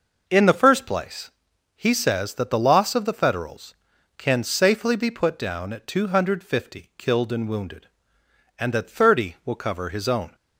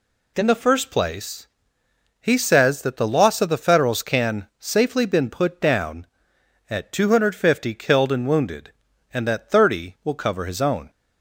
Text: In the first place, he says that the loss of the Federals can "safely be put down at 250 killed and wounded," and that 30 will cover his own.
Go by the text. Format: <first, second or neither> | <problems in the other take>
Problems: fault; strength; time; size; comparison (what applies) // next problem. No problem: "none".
first | says "been" for "be"; at 5.0 s